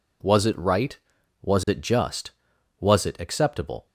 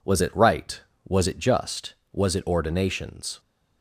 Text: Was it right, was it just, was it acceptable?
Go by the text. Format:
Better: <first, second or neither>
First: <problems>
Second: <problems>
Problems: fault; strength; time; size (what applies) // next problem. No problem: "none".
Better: first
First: none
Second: says "ordinations" for "acceptable"; at 2.4 s